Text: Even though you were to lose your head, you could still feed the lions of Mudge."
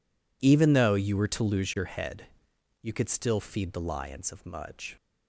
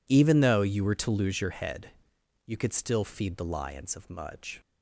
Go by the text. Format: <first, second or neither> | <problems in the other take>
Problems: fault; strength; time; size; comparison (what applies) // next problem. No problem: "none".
neither | none